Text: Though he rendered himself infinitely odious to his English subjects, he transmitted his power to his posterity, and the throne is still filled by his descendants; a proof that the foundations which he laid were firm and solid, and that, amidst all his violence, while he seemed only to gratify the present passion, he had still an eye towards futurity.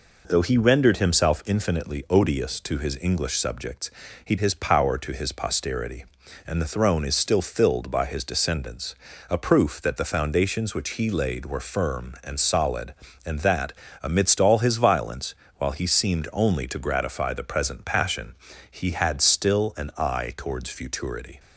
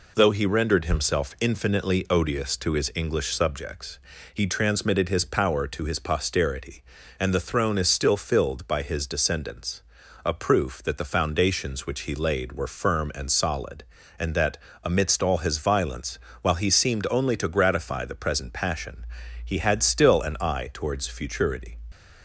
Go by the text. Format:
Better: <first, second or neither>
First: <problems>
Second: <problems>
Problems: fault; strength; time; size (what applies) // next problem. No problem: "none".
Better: second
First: skips "transmitted"; at 4.3 s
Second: none